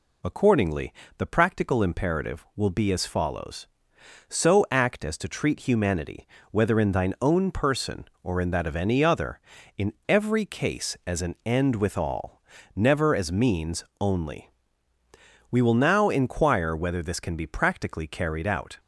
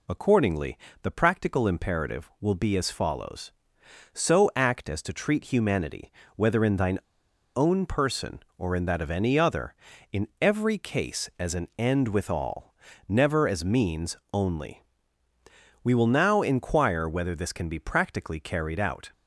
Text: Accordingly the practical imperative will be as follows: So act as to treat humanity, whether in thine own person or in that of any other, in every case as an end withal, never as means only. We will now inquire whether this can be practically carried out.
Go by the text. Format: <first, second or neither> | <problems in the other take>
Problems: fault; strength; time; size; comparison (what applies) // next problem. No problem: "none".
first | pauses between "Accordingly" and "the"; slight; at 0.7 s; 0.24 s long; slight in the first // pauses between "thine" and "own"; noticeable; at 6.9 s; 0.58 s long // pauses between "means" and "only"; slight; at 14.1 s; 0.16 s long; slight in the first